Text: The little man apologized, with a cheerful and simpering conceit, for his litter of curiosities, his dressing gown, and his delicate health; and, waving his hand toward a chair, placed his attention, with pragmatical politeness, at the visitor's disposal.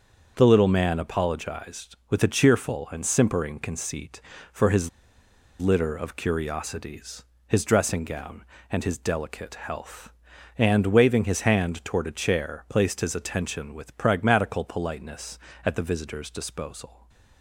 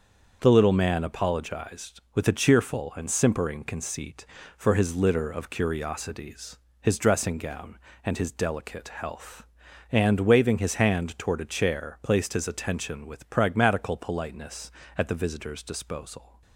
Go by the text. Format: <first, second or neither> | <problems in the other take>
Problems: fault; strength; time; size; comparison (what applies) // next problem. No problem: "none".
second | starts louder than the rest; until 1.3 s; 6.5 dB; also in the second // pauses between "his" and "litter"; noticeable; at 4.8 s; 0.71 s long // stays silent after the last word; slight; from 16.8 s on; 0.6 s long